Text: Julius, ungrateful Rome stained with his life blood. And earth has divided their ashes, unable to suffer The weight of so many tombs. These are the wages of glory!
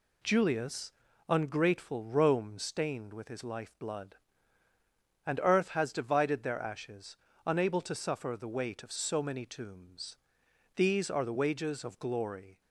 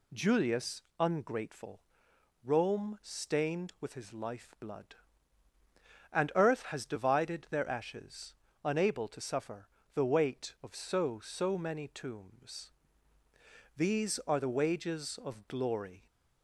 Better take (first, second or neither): first